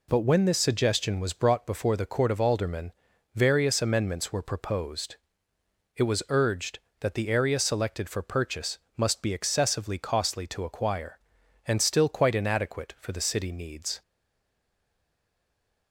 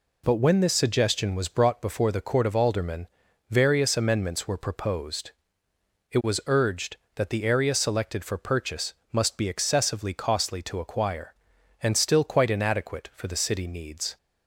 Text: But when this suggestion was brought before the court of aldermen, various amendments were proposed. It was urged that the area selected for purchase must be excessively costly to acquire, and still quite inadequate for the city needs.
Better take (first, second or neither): second